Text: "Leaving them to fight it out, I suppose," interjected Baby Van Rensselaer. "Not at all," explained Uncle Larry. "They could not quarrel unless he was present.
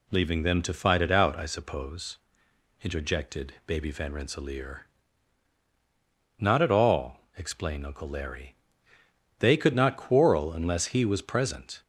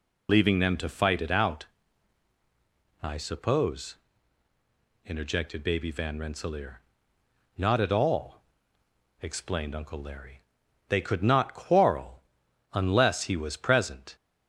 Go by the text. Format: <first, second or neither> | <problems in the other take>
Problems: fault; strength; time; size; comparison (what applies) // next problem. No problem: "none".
first | loses the start of "Leaving"; at 0.2 s; 55 ms // pauses between "quarrel" and "unless"; noticeable; at 12.2 s; 0.48 s long